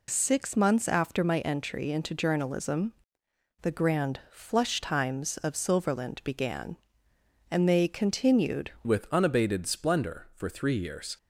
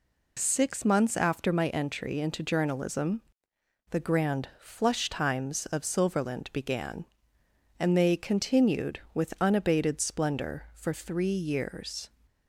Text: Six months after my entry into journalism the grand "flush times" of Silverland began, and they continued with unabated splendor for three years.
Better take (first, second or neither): second